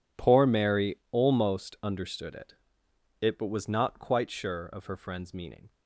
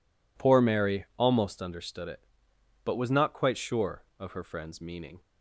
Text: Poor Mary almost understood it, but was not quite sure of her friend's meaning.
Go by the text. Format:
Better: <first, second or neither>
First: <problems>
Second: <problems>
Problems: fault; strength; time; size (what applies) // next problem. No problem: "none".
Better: second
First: says "it" twice; at 3.2 s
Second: none